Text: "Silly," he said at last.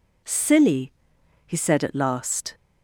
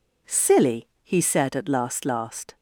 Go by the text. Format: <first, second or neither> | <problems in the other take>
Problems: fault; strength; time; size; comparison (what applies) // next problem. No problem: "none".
first | says "last" twice; at 2.0 s